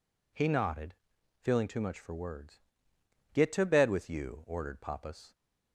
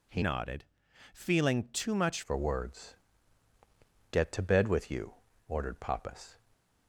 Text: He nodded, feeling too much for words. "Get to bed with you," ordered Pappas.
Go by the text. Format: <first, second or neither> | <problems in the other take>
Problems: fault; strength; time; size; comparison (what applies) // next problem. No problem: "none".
first | changes voice from "nodded" to "much"; from 0.2 to 2.2 s; 2.0 s long // stays silent after the last word; slight; from 6.3 s on; 0.5 s long